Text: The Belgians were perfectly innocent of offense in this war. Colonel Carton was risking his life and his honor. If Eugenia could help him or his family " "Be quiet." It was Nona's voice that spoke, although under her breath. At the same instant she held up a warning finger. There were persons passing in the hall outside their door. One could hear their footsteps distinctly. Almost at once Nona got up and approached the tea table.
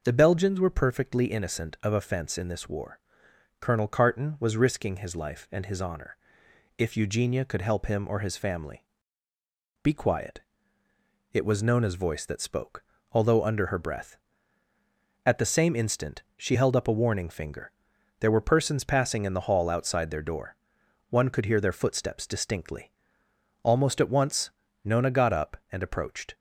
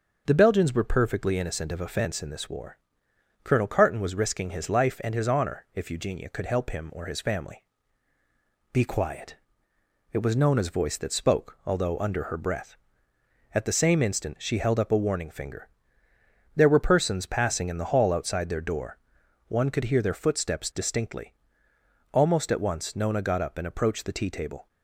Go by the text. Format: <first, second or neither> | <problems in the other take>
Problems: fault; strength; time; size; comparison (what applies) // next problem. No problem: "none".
second | starts louder than the rest; until 1.0 s; 6.5 dB; strong in the second // pauses between "instant" and "she"; slight; at 16.2 s; 0.16 s long // pauses between "once" and "Nona"; slight; at 24.5 s; 0.34 s long // stops before "the tea table"; at 26.3 s